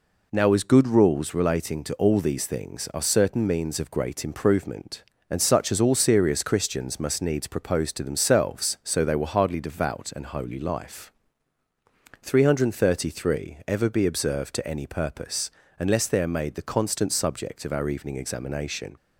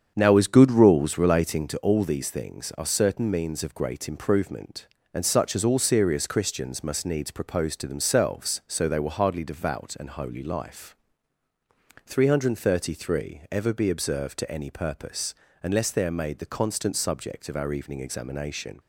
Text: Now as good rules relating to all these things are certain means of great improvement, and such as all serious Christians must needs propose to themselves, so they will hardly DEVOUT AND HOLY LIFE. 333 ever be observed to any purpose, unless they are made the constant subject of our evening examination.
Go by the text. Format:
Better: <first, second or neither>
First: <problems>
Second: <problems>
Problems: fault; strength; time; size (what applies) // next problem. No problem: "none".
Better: first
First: none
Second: starts louder than the rest; strong; until 1.8 s; 7.5 dB